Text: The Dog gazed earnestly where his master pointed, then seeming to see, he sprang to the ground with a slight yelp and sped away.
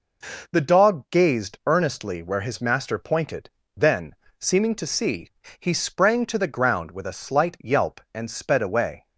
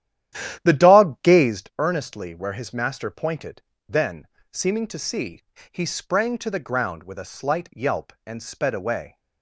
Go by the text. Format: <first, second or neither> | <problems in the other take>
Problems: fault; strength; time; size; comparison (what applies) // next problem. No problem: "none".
first | starts louder than the rest; strong; until 1.6 s; 11.5 dB // pauses between "then" and "seeming"; slight; at 4.2 s; 0.24 s long; slight in the first